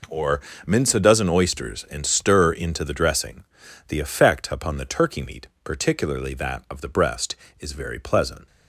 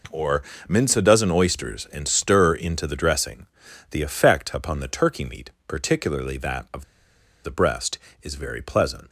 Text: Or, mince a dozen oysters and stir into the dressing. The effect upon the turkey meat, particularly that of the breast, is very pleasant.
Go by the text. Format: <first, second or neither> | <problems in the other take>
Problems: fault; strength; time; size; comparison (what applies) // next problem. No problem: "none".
first | pauses between "of" and "the"; noticeable; at 6.8 s; 0.60 s long